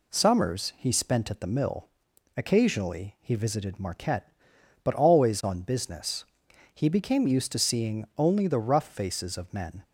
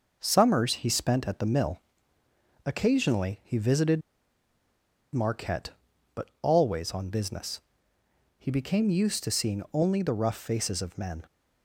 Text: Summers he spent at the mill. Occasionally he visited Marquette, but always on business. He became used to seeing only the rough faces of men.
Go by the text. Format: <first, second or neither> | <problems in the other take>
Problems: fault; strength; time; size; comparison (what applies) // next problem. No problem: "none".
first | pauses between "visited" and "Marquette"; at 4.0 s; 1.1 s long